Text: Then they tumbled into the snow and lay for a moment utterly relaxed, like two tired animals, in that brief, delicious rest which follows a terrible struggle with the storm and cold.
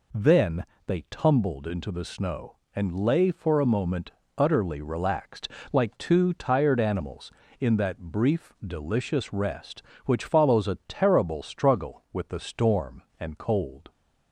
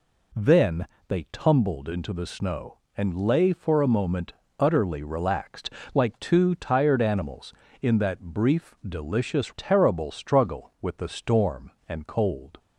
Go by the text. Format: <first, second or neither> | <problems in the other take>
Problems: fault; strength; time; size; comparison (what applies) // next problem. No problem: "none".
first | pauses between "Then" and "they"; slight; at 0.8 s; 0.22 s long; slight in the first // pauses between "moment" and "utterly"; slight; at 4.3 s; 0.26 s long; slight in the first // skips "rest which follows a"; at 9.5 s